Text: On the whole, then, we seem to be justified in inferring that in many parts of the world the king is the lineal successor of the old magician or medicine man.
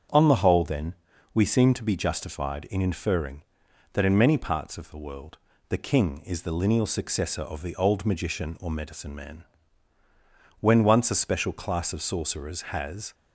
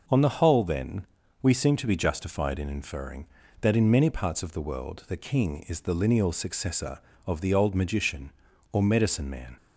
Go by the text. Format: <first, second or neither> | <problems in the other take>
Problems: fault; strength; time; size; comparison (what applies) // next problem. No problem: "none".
second | starts louder than the rest; strong; until 1.5 s; 7.5 dB // pauses between "world" and "the"; slight; at 5.3 s; 0.30 s long // goes on to say "When once a special class of sorcerers has"; strong; from 10.5 s on; 2.5 s long